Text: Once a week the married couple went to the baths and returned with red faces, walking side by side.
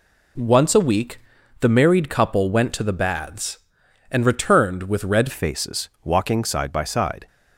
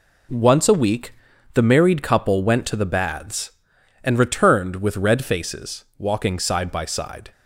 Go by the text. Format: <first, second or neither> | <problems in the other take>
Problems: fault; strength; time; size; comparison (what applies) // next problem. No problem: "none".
second | pauses between "week" and "the"; at 1.1 s; 0.42 s long; also in the second // changes voice at "faces"; from 5.3 s on; 1.9 s long